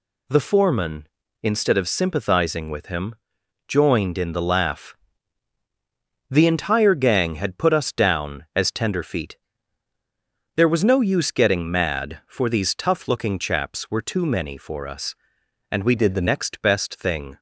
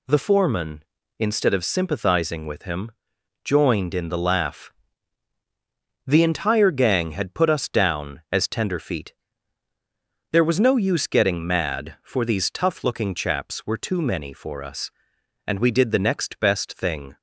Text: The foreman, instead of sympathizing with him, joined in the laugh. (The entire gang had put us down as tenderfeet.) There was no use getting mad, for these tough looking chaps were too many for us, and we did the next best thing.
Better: second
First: changes voice from "did" to "the"; from 15.9 to 16.2 s; 0.3 s long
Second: none

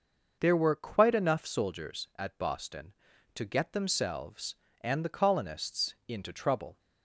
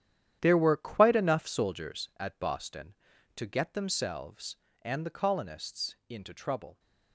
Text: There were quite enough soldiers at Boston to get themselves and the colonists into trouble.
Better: first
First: none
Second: gets quieter; strong; throughout; 12.5 dB

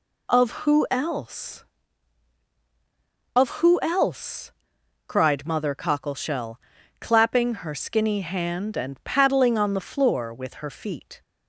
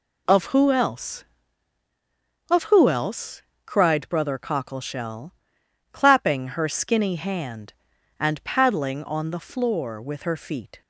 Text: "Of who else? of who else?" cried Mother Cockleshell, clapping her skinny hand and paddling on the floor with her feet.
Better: first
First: none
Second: says "Brother" for "Mother"; at 4.0 s

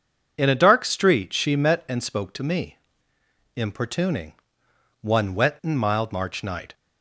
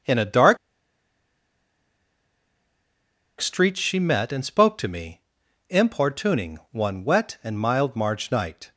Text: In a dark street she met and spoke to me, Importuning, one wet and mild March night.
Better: first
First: none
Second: starts louder than the rest; until 3.8 s; 6.5 dB // pauses between "dark" and "street"; strong; at 0.5 s; 2.8 s long

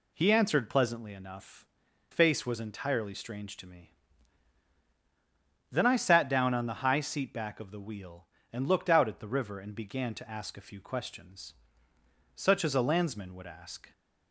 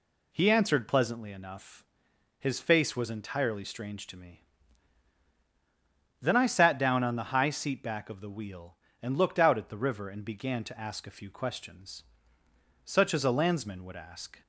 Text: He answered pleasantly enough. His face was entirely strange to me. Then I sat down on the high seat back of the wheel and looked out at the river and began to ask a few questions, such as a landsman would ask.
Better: second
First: skips "His"; at 1.8 s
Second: none

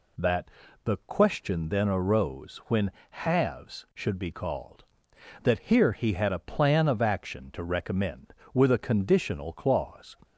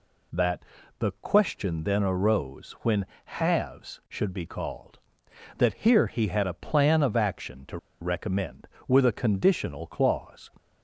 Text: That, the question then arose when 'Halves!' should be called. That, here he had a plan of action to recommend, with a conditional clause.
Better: first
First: pauses between "when" and "Halves"; slight; at 2.8 s; 0.20 s long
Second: pauses between "when" and "Halves"; slight; at 3.0 s; 0.20 s long // pauses between "to" and "recommend"; slight; at 7.7 s; 0.24 s long

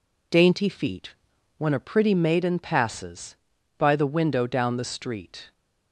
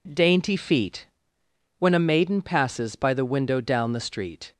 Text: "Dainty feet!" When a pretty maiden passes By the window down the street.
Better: first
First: none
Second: skips "pretty"; at 1.9 s

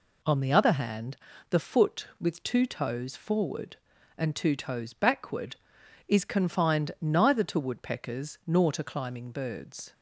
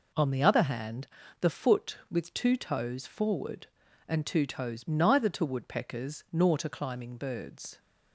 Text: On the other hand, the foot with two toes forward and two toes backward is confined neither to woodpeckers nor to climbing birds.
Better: first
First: none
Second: skips "backward is confined"; at 4.8 s

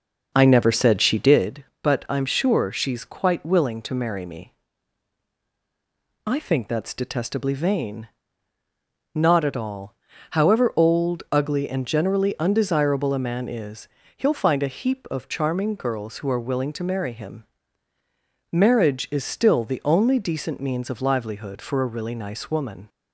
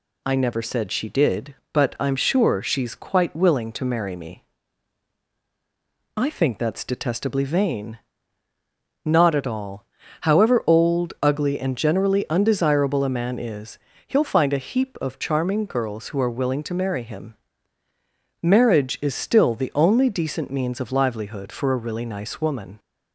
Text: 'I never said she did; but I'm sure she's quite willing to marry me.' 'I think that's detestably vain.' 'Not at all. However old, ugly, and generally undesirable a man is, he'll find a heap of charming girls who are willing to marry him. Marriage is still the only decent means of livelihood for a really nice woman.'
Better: second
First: starts louder than the rest; noticeable; until 1.5 s; 6 dB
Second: none

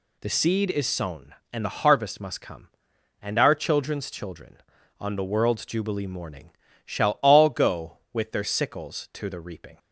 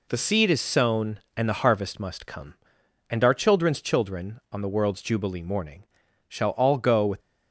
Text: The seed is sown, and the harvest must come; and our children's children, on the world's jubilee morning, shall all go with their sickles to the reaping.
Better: first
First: none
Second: stops before "their sickles to the reaping"; at 7.1 s

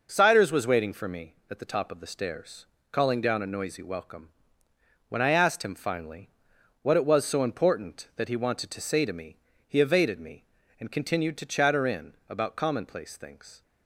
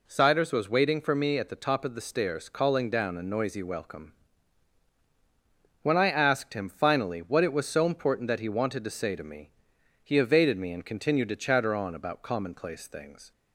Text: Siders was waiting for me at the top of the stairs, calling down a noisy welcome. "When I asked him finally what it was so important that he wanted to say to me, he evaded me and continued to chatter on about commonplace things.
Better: second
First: pauses between "finally" and "what"; noticeable; at 6.2 s; 0.52 s long // says "in" for "on"; at 11.8 s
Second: none

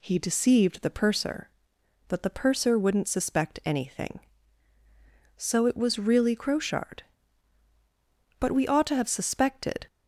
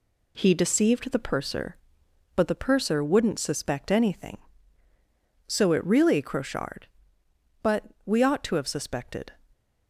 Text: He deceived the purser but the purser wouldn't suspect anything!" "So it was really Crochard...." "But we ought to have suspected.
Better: first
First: none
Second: skips "was"; at 5.8 s // pauses between "But" and "we"; slight; at 7.8 s; 0.20 s long

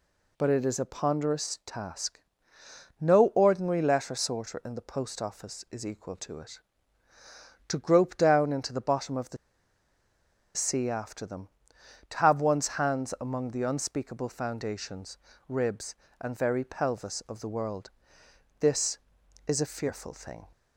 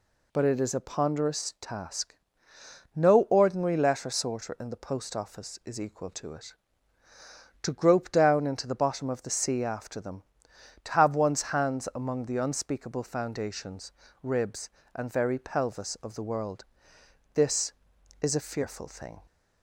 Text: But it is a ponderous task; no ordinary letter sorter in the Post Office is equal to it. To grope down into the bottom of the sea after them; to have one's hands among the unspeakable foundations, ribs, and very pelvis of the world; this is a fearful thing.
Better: second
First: pauses between "the" and "sea"; at 9.3 s; 1.1 s long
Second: none

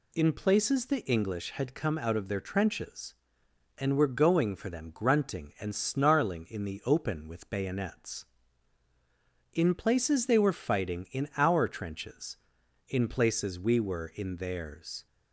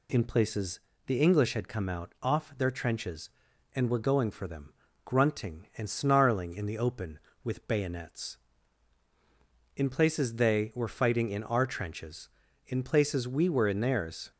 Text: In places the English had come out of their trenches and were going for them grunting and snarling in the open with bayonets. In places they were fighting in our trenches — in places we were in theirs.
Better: first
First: none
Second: pauses between "places" and "the"; slight; at 0.8 s; 0.26 s long // says "off" for "of"; at 2.2 s // pauses between "them" and "grunting"; slight; at 4.7 s; 0.32 s long

